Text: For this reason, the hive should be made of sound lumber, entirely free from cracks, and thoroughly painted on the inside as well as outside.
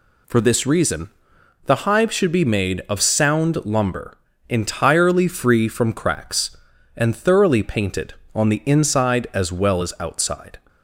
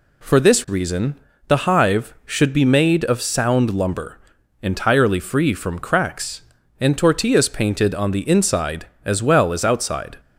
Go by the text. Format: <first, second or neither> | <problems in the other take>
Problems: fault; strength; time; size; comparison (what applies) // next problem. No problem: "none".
first | says "tortillas" for "thoroughly"; at 6.9 s